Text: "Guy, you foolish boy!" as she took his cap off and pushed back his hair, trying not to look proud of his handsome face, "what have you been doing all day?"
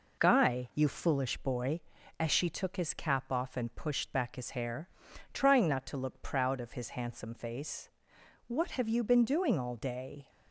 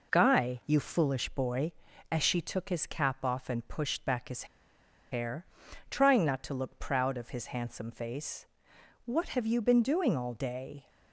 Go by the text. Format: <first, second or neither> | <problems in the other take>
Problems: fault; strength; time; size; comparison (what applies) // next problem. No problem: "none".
first | pauses between "his" and "hair"; noticeable; at 4.4 s; 0.66 s long